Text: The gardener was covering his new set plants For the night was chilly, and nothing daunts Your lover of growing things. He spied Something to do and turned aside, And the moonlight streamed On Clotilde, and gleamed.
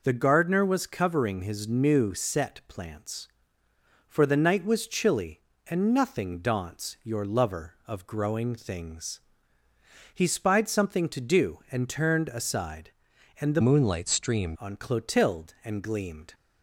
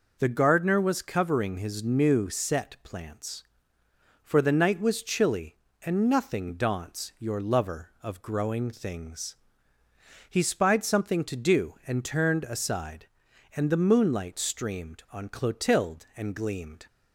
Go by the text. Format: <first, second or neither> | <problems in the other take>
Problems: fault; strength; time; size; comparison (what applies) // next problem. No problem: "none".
second | changes voice from "moonlight" to "streamed"; from 13.6 to 14.5 s; 0.9 s long